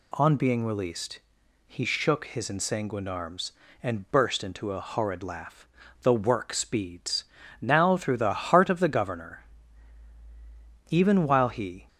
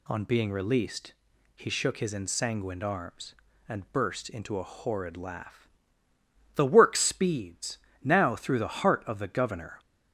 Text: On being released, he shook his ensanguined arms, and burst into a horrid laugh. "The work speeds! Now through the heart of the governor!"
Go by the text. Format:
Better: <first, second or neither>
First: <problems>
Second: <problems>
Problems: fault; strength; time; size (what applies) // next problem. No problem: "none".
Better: second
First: goes on to say "Even while he"; noticeable; from 10.8 s on; 0.98 s long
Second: none